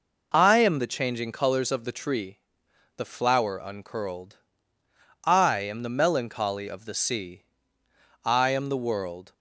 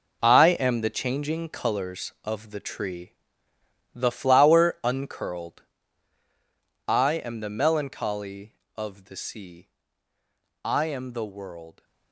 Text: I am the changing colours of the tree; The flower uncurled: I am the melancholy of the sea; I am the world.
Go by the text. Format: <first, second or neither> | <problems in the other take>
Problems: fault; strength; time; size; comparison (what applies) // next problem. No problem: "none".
first | gets quieter; strong; throughout; 11 dB